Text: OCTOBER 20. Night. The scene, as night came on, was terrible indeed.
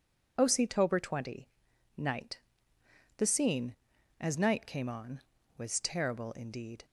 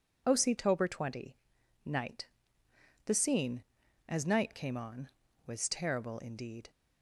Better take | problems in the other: neither | none

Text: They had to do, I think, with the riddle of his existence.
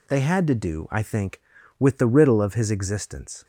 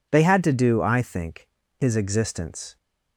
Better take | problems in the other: first | skips "with the riddle of"; at 1.6 s

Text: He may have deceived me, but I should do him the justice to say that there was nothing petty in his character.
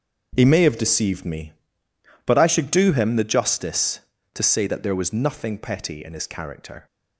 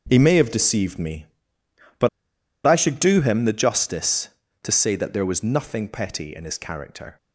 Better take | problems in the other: first | starts louder than the rest; until 1.1 s; 7 dB; also in the first // pauses between "but" and "I"; noticeable; at 2.0 s; 0.57 s long

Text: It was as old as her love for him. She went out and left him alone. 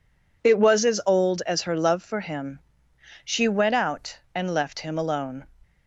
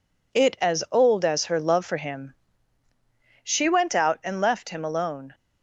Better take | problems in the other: first | skips "was"; at 0.5 s

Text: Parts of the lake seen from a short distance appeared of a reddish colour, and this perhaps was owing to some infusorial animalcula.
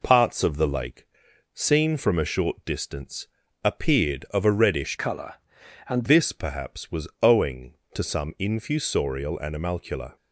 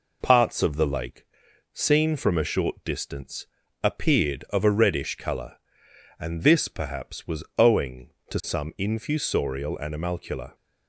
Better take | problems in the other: second | pauses between "lake" and "seen"; noticeable; at 1.0 s; 0.48 s long; noticeable in the second // pauses between "distance" and "appeared"; slight; at 3.2 s; 0.34 s long; slight in the second // changes voice from "colour" to "and"; from 4.9 to 6.0 s; 1.1 s long

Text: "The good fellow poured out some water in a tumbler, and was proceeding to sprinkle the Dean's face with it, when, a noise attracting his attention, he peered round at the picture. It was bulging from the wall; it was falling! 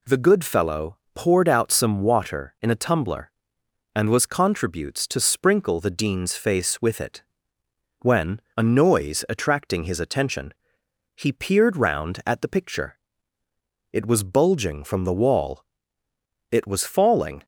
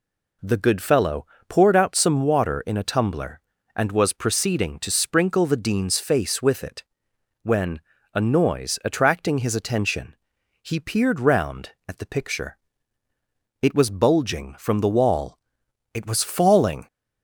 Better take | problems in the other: second | pauses between "fellow" and "poured"; slight; at 0.9 s; 0.16 s long; slight in the second // says "contributes" for "proceeding"; at 4.2 s

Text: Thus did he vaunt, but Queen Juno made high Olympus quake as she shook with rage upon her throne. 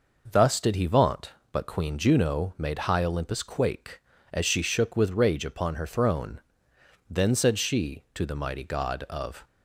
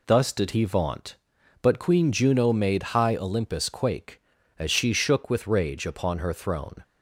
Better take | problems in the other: second | goes on to say "Then said she to the mighty god of"; strong; from 7.0 s on; 2.3 s long

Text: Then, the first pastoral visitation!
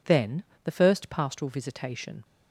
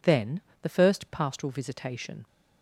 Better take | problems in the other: neither | none

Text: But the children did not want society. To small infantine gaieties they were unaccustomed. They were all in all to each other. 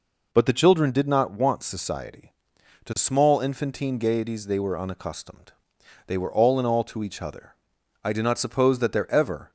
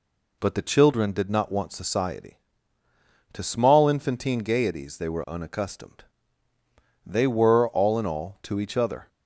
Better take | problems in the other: second | goes on to say "I do not suppose that there ever"; from 8.0 s on; 1.4 s long

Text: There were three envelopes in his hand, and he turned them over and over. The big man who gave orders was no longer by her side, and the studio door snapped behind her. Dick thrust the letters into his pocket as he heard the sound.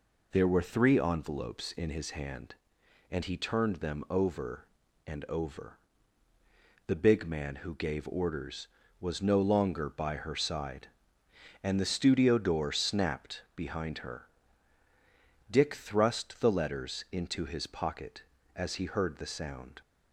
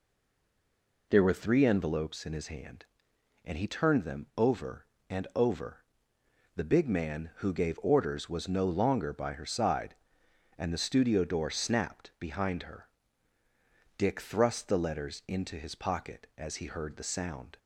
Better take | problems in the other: first | stays silent before the first word; until 1.0 s; 1.0 s long

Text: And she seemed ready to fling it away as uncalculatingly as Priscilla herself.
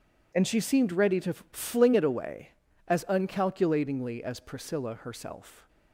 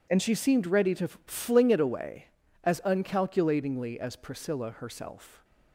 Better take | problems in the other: neither | pauses between "to" and "fling"; slight; the same in both

